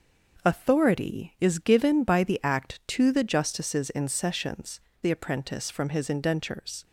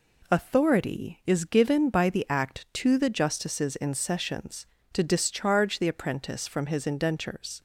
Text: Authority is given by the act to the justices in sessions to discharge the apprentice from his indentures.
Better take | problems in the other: second | starts louder than the rest; noticeable; until 1.5 s; 6 dB // skips "to discharge"; at 4.9 s

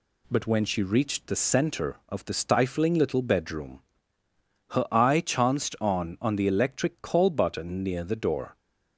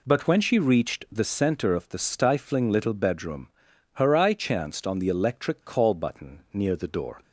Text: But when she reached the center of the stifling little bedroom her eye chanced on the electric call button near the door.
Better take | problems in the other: second | pauses between "bedroom" and "her"; noticeable; at 3.8 s; 0.90 s long; noticeable in the second // says "on" twice; at 6.1 s

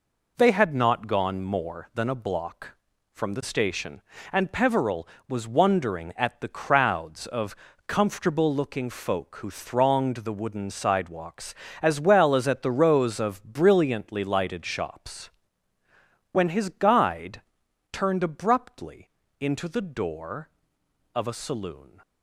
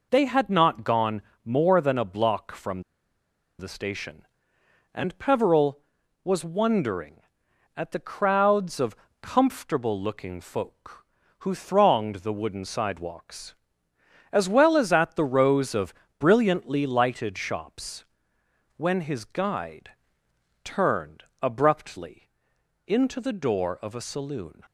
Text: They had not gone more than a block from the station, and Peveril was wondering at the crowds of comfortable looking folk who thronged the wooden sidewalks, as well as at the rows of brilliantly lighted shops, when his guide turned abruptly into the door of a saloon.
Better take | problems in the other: first | pauses between "gone" and "more"; slight; at 1.2 s; 0.24 s long // pauses between "from" and "the"; noticeable; at 2.8 s; 0.76 s long // pauses between "of" and "comfortable"; slight; at 8.9 s; 0.26 s long; slight in the first // pauses between "of" and "brilliantly"; slight; at 15.9 s; 0.26 s long // pauses between "guide" and "turned"; noticeable; at 19.9 s; 0.72 s long; noticeable in the first // pauses between "turned" and "abruptly"; slight; at 21.2 s; 0.18 s long // pauses between "abruptly" and "into"; noticeable; at 22.2 s; 0.58 s long; slight in the first

